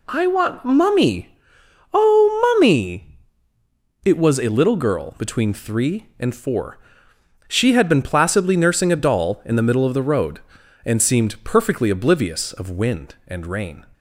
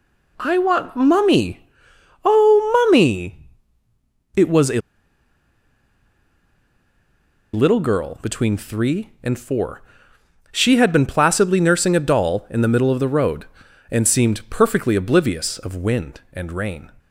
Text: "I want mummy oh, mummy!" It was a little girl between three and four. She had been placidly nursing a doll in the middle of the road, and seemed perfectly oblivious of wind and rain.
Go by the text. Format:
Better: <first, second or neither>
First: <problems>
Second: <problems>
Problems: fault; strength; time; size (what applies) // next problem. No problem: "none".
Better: first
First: pauses between "mummy" and "oh"; noticeable; at 1.2 s; 0.62 s long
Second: pauses between "mummy" and "oh"; noticeable; at 1.5 s; 0.62 s long // pauses between "a" and "little"; strong; at 4.7 s; 2.7 s long